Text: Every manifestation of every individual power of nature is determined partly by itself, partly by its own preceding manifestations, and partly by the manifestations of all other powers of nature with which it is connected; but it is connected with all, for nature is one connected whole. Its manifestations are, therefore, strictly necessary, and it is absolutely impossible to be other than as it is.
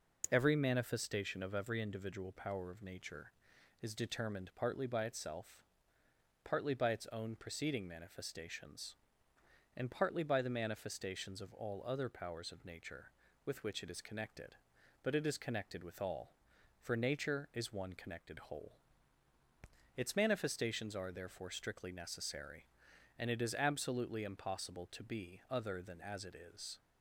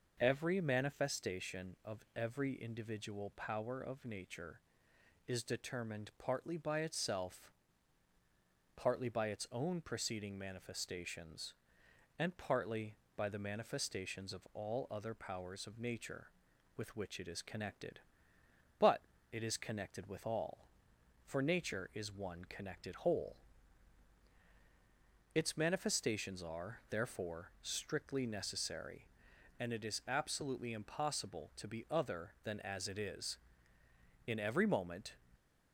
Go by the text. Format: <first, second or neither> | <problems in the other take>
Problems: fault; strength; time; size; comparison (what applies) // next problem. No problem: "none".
first | pauses between "but" and "it"; slight; at 19.0 s; 0.28 s long // goes on to say "In every moment"; noticeable; from 34.2 s on; 0.90 s long